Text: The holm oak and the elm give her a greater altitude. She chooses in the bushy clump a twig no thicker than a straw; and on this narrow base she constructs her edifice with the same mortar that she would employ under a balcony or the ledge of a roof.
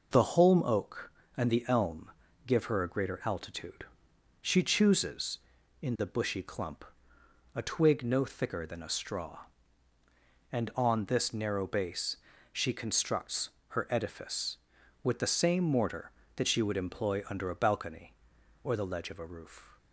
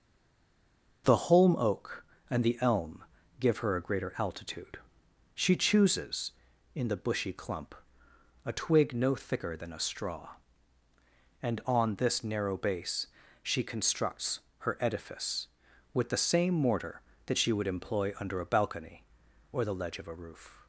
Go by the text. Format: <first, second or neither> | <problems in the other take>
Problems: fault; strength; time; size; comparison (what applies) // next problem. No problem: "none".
first | stays silent before the first word; until 1.0 s; 1.0 s long // pauses between "elm" and "give"; slight; at 3.0 s; 0.36 s long; slight in the first // pauses between "clump" and "a"; noticeable; at 7.7 s; 0.68 s long; noticeable in the first // pauses between "base" and "she"; at 13.0 s; 0.38 s long; also in the first // pauses between "constructs" and "her"; slight; at 14.3 s; 0.20 s long; slight in the first